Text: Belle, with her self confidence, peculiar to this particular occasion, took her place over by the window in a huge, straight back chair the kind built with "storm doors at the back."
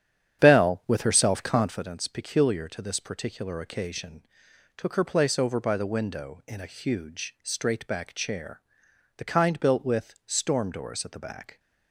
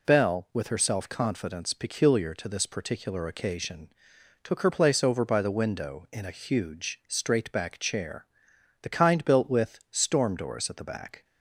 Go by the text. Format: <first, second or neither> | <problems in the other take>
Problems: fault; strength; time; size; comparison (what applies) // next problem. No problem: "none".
second | starts louder than the rest; strong; until 1.9 s; 9 dB // pauses between "chair" and "the"; noticeable; at 8.6 s; 0.56 s long; noticeable in the second